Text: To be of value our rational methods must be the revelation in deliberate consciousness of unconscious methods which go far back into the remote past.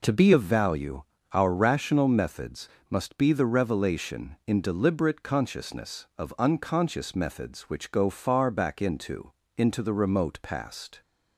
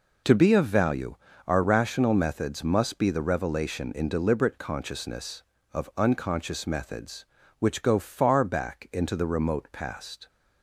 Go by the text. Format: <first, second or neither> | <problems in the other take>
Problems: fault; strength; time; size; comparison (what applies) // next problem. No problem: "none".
second | pauses between "value" and "our"; slight; at 1.0 s; 0.28 s long; slight in the second // pauses between "methods" and "must"; slight; at 2.6 s; 0.22 s long // says "into" twice; at 9.5 s